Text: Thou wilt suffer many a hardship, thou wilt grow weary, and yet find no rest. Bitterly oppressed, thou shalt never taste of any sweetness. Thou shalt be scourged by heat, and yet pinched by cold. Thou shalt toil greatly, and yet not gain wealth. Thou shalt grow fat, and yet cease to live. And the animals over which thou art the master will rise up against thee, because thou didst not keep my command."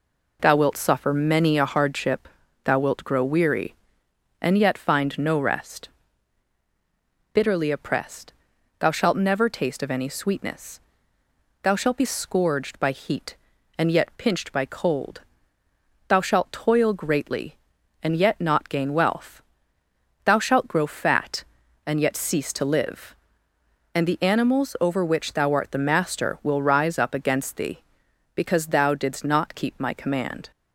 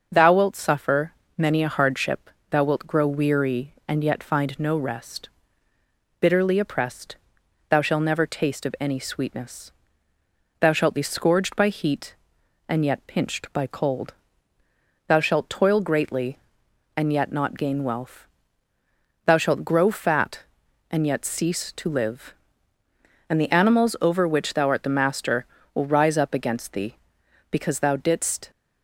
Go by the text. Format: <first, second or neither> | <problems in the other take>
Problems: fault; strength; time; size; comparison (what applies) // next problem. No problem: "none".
first | starts louder than the rest; until 1.1 s; 6.5 dB // pauses between "suffer" and "many"; slight; at 1.1 s; 0.24 s long // stops before "not keep my command"; at 28.5 s